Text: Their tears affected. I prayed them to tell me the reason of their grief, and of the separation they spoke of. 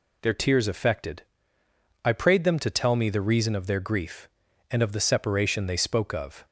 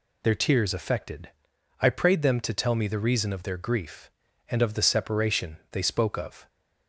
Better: neither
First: none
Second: none

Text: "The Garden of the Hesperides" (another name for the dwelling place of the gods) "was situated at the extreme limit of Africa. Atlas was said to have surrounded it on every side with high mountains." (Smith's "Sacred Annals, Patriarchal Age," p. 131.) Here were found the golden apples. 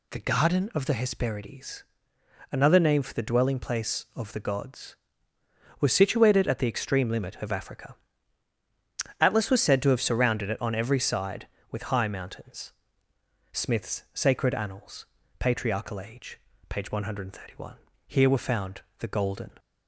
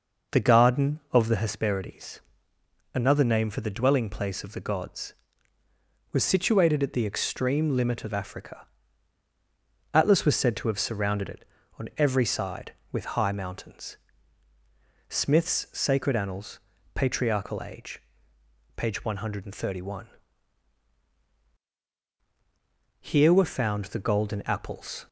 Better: second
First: pauses between "found" and "the"; slight; at 18.8 s; 0.16 s long // stops before "apples"; at 19.5 s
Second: none

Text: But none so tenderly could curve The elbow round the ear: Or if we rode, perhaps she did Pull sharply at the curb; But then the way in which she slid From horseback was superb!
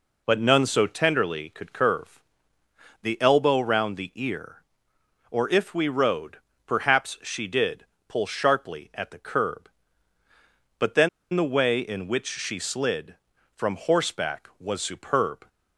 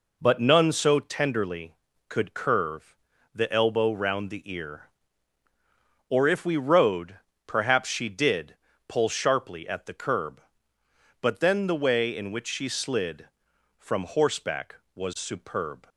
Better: second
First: pauses between "curve" and "The"; noticeable; at 2.2 s; 0.80 s long // pauses between "did" and "Pull"; slight; at 7.8 s; 0.24 s long // pauses between "then" and "the"; slight; at 11.0 s; 0.24 s long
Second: pauses between "curve" and "The"; slight; at 2.9 s; 0.36 s long // pauses between "did" and "Pull"; slight; at 8.5 s; 0.34 s long

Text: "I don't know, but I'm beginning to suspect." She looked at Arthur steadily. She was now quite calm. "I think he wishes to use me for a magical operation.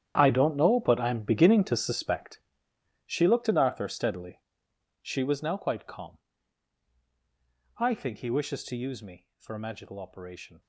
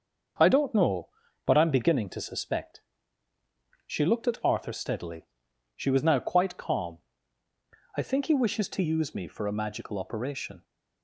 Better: second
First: gets quieter; strong; throughout; 15 dB // starts louder than the rest; strong; until 1.1 s; 10 dB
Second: starts louder than the rest; until 1.7 s; 6.5 dB

